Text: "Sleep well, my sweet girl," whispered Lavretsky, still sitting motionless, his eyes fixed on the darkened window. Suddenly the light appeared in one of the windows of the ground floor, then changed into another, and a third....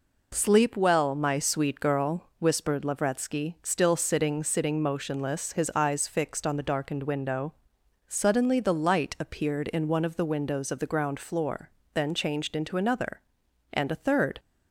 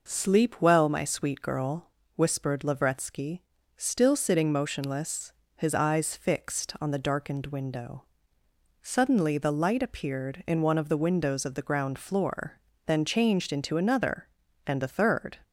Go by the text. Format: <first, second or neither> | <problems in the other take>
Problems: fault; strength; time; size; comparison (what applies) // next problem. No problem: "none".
second | says "sitting" twice; at 4.4 s